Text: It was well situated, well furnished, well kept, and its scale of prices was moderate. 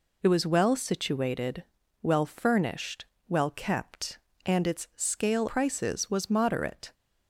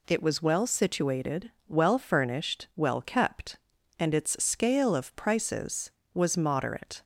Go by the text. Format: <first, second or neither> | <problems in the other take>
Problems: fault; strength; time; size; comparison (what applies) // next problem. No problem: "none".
second | skips "of"; at 5.4 s